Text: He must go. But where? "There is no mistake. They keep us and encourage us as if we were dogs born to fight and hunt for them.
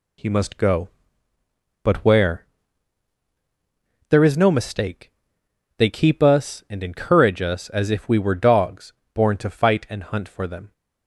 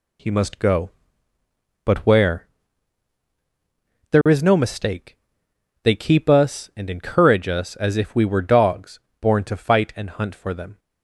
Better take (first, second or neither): neither